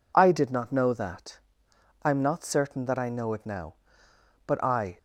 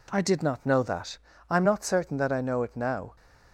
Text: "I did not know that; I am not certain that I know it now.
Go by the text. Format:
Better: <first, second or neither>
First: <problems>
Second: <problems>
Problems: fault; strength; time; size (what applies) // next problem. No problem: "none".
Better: second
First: goes on to say "But I"; from 4.4 s on; 0.52 s long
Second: none